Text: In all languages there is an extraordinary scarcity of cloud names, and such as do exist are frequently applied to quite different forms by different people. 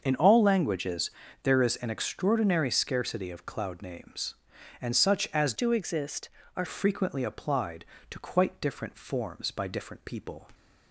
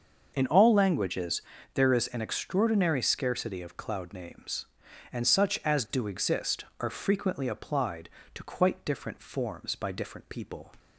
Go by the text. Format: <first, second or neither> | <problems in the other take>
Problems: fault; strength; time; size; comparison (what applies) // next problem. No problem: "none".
second | starts louder than the rest; until 1.0 s; 6.5 dB; also in the second // pauses between "languages" and "there"; slight; at 1.1 s; 0.32 s long; slight in the second // changes voice from "do" to "are"; from 5.5 to 6.6 s; 1.1 s long